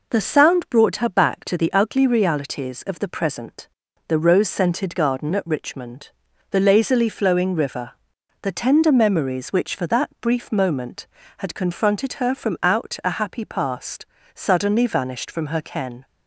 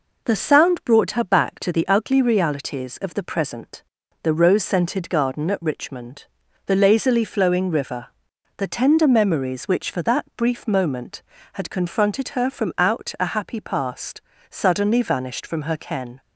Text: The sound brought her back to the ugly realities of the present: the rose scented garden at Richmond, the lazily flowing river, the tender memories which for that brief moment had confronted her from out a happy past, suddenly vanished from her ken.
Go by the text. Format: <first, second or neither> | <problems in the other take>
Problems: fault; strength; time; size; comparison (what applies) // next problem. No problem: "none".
neither | none